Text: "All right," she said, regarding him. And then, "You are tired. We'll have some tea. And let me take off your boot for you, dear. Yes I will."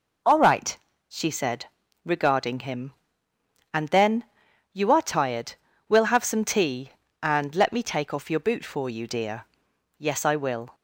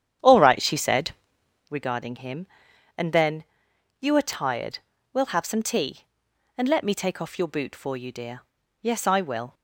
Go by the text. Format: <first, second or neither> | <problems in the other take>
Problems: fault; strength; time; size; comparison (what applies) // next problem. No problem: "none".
first | starts louder than the rest; strong; until 1.8 s; 9.5 dB